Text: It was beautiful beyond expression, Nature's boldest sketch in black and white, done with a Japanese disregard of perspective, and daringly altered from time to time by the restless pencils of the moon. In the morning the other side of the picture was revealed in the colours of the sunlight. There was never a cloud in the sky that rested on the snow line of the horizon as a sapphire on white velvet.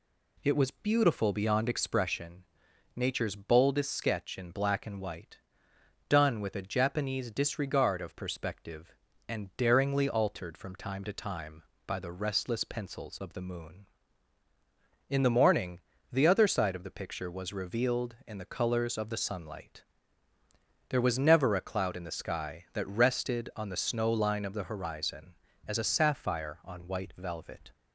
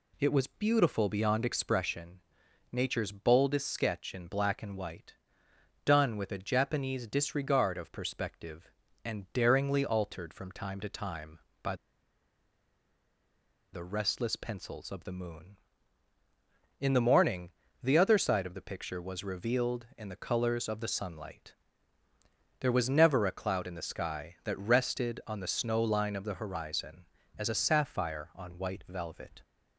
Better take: first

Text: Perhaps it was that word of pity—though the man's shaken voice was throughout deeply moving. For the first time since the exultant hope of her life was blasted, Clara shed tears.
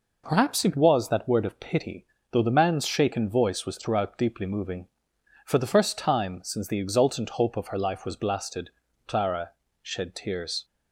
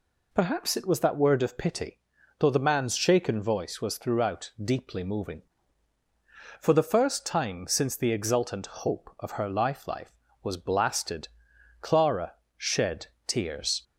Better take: first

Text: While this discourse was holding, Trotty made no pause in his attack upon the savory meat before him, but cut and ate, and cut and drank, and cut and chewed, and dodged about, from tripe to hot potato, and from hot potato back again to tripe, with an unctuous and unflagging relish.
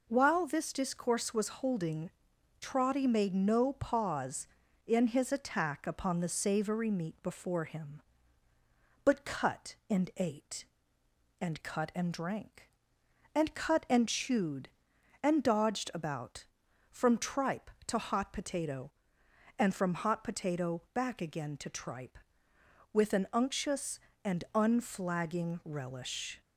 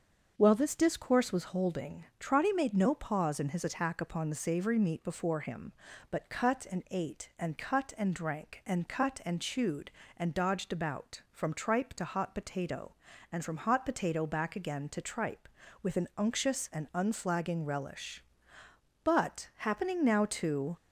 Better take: first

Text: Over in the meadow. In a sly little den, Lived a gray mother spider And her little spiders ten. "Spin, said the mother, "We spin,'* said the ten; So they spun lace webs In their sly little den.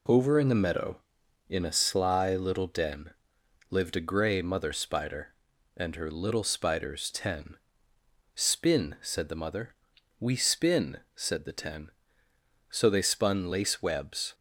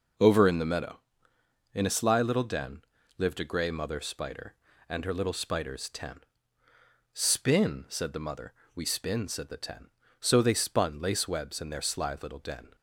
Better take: second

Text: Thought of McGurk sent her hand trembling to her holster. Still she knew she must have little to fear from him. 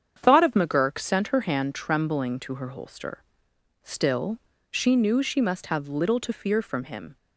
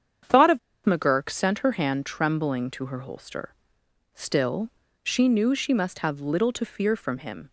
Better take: first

